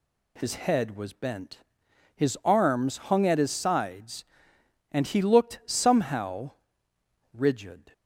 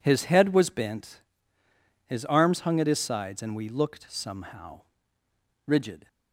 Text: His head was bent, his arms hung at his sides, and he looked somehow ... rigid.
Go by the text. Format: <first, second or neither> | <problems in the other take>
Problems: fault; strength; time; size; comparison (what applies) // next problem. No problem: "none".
first | says "we" for "he"; at 3.5 s